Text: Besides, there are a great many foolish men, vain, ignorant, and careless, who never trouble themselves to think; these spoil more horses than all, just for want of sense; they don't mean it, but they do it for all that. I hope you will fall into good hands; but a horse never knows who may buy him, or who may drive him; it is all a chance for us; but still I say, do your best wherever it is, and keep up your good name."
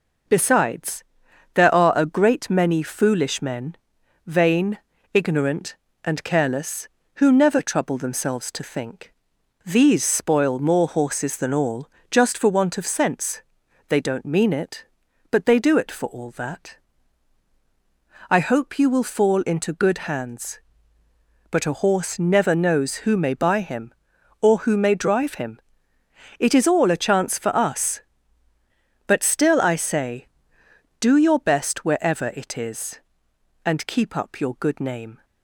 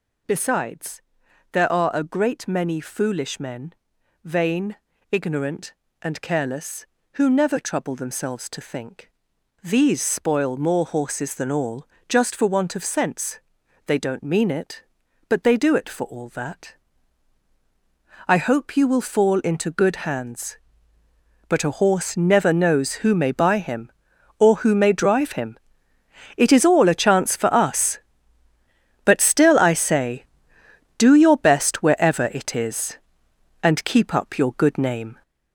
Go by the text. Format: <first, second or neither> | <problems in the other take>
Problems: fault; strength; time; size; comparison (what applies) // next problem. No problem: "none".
first | gets louder; throughout; 7 dB